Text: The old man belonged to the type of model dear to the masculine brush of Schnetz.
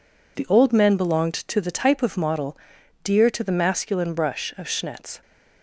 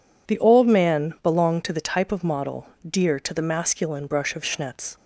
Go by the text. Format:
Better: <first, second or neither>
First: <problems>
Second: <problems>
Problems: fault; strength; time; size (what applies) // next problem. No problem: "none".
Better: second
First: says "men" for "man"; at 0.7 s // pauses between "model" and "dear"; noticeable; at 2.5 s; 0.48 s long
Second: pauses between "model" and "dear"; slight; at 2.6 s; 0.24 s long